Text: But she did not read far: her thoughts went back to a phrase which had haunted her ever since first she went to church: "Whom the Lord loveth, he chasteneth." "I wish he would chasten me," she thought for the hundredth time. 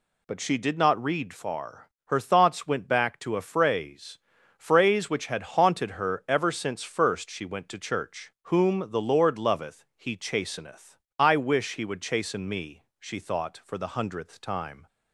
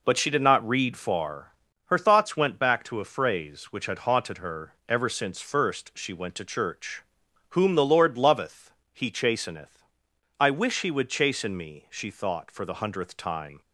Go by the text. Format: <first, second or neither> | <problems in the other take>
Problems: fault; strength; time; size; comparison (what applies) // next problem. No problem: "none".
second | says "phrase" twice; at 4.5 s